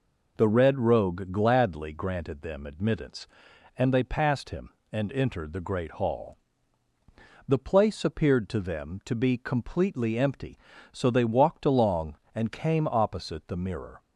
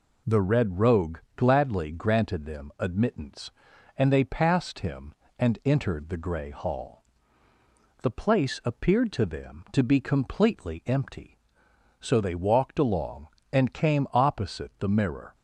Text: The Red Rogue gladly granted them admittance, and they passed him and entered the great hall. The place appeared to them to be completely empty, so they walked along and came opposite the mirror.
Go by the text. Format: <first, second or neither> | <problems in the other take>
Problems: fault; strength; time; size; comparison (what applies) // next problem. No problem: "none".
first | pauses between "Rogue" and "gladly"; slight; at 1.1 s; 0.18 s long // says "grey" for "great"; at 6.1 s